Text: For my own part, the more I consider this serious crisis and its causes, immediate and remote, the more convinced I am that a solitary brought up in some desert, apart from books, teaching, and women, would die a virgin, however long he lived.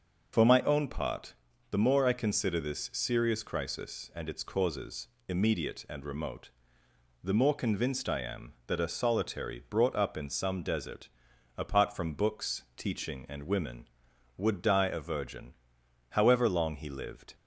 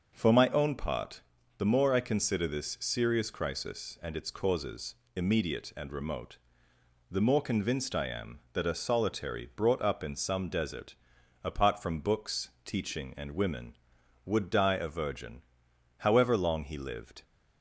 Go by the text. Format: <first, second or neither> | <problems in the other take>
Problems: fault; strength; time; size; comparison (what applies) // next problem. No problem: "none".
second | loses the start of "For"; at 0.3 s; 65 ms